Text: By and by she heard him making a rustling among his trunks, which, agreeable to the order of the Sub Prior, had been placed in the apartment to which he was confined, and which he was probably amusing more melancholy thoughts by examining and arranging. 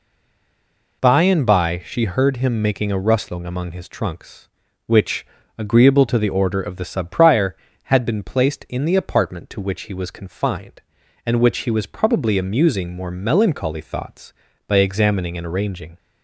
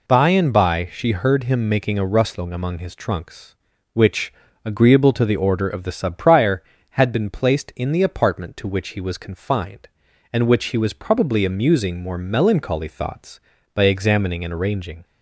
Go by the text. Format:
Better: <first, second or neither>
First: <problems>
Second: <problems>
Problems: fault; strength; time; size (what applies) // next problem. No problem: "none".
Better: second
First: stays silent before the first word; until 1.0 s; 1.0 s long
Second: none